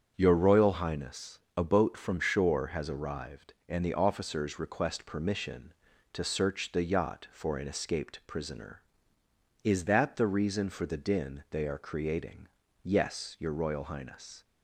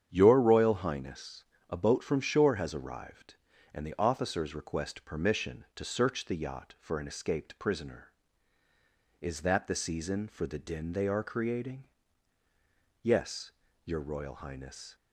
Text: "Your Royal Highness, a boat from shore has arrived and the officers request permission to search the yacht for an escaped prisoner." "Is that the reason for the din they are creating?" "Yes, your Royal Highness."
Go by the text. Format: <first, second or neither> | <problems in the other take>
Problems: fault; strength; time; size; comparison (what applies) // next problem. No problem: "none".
first | starts louder than the rest; strong; until 1.1 s; 8.5 dB; strong in the first // says "season" for "reason"; at 9.7 s